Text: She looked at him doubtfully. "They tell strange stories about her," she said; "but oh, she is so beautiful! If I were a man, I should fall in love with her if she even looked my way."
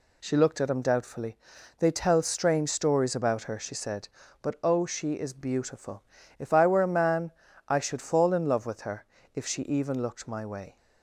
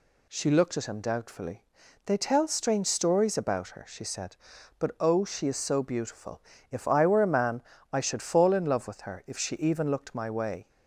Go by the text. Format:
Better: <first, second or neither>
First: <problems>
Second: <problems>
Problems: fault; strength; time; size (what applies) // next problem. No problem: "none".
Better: second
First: skips "so"; at 5.3 s // pauses between "her" and "if"; slight; at 9.0 s; 0.28 s long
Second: none